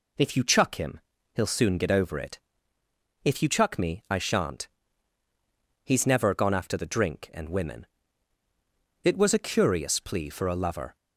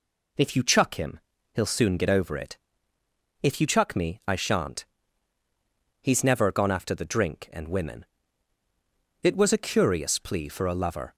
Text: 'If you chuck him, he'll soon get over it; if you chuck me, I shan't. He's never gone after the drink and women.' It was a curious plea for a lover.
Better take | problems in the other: neither | none

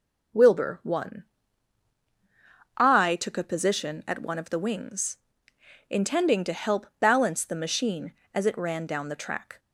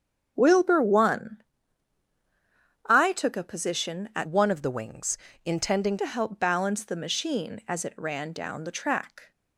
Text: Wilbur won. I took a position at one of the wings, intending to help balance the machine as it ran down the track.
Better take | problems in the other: first | starts louder than the rest; strong; until 1.3 s; 7.5 dB // changes voice from "one" to "intending"; from 4.2 to 5.9 s; 1.7 s long

